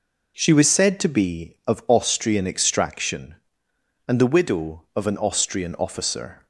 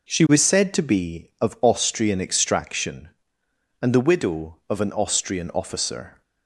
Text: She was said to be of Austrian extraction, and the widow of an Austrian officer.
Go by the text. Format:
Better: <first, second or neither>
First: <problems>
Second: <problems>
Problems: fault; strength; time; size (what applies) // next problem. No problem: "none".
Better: neither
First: none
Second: none